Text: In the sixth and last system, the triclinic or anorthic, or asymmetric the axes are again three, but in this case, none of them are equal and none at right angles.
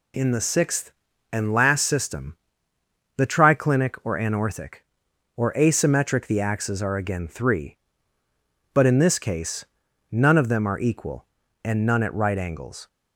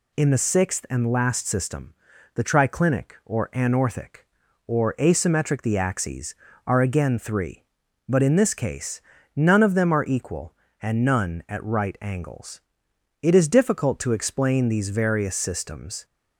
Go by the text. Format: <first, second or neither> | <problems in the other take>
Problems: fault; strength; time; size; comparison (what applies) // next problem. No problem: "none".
first | goes on to say "It is difficult to explain these various systems"; strong; from 13.2 s on; 2.8 s long